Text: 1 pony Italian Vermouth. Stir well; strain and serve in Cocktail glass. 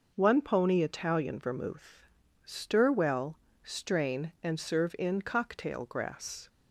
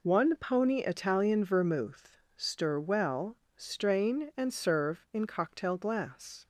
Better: second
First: says "grass" for "glass"; at 5.8 s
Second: none

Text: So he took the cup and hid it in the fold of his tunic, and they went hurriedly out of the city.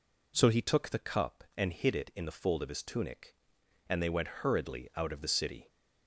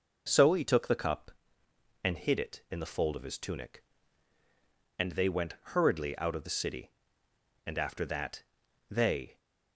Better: first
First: none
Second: pauses between "went" and "hurriedly"; slight; at 5.5 s; 0.16 s long // goes on to say "And after that they"; strong; from 7.6 s on; 1.7 s long

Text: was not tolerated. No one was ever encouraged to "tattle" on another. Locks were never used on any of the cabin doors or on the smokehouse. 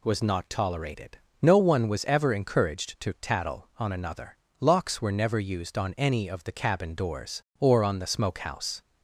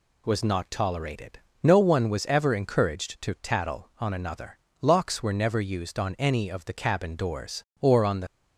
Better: first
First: none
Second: stops before "smokehouse"; at 8.2 s

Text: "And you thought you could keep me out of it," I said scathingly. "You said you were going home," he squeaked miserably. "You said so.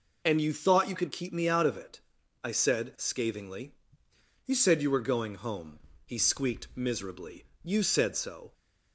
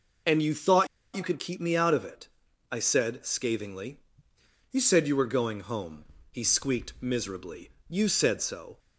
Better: first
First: none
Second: pauses between "thought" and "you"; slight; at 0.8 s; 0.29 s long

